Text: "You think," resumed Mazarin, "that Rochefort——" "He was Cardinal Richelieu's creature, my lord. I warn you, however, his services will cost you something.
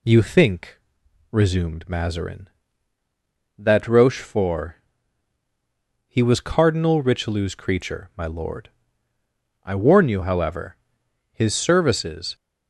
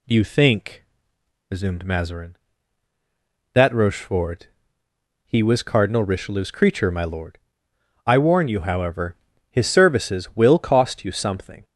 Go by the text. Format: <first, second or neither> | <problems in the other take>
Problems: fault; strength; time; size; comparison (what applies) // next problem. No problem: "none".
second | stops before "will cost you something"; at 12.3 s